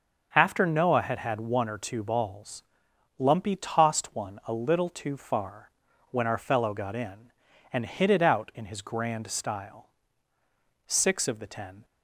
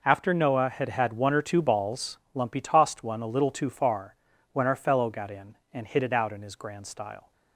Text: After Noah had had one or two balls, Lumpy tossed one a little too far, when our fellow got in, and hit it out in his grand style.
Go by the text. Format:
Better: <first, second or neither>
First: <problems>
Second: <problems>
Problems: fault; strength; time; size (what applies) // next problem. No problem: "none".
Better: second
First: starts louder than the rest; until 1.3 s; 6.5 dB // goes on to say "Six of the ten"; noticeable; from 10.8 s on; 0.98 s long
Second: none